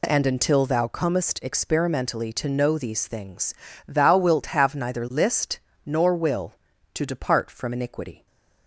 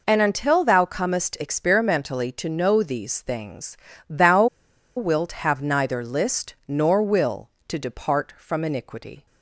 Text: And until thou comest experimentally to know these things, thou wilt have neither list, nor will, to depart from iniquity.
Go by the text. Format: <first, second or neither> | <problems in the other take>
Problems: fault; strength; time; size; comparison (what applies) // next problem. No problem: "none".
first | pauses between "thou" and "wilt"; noticeable; at 4.4 s; 0.50 s long